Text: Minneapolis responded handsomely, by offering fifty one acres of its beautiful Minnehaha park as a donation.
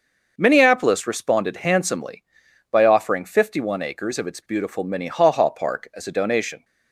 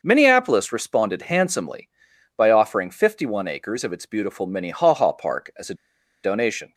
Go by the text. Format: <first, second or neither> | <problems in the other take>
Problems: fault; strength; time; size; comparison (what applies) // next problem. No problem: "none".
first | starts louder than the rest; noticeable; until 1.0 s; 6 dB; noticeable in the first // pauses between "a" and "donation"; noticeable; at 5.7 s; 0.48 s long